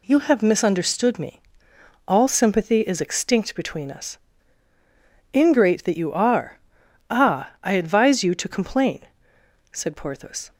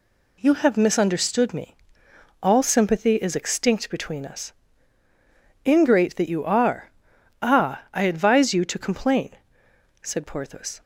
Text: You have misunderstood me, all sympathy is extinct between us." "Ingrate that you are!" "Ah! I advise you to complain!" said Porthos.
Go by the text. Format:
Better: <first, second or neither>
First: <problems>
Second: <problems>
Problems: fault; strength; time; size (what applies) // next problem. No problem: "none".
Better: neither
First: none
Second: none